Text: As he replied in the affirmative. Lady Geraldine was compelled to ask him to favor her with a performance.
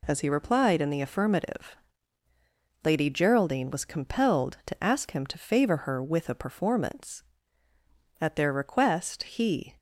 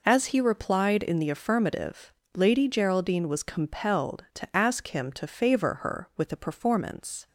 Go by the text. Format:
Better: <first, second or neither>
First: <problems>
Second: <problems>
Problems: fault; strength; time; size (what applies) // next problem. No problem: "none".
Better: second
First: goes on to say "At their request he"; from 8.1 s on; 1.5 s long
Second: none